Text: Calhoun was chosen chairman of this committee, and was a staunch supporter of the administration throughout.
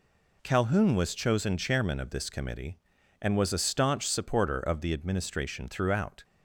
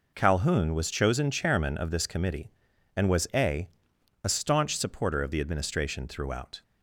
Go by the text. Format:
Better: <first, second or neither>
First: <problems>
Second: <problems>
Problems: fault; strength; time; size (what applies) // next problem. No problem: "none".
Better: first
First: none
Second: says "a" twice; at 4.2 s